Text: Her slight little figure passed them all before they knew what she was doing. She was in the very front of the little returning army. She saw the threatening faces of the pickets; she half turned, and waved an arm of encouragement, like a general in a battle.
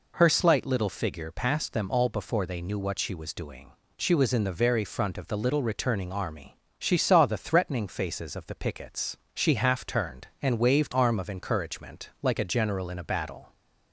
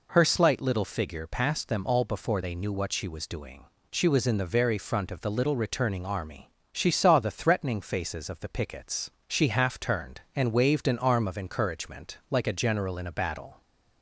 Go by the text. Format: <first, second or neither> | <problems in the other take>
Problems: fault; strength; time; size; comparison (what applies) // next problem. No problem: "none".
second | skips "an"; at 10.9 s